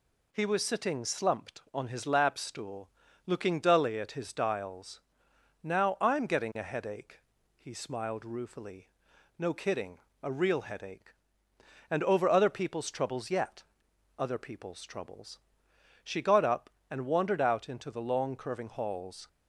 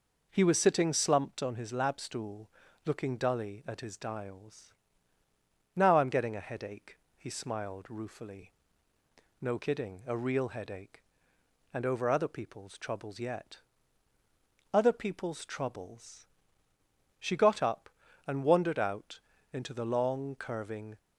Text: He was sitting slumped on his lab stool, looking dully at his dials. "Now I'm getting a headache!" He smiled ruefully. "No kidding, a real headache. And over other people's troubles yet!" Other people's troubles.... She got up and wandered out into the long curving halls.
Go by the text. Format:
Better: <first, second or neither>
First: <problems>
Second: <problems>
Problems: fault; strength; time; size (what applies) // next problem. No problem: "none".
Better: first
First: none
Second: pauses between "out" and "into"; slight; at 19.1 s; 0.36 s long // stops before "halls"; at 20.9 s